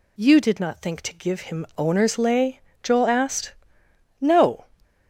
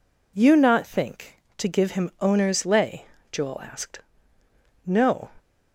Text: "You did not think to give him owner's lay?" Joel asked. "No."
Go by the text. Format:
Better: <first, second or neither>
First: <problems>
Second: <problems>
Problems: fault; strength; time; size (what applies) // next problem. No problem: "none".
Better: first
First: none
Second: skips "did"; at 0.5 s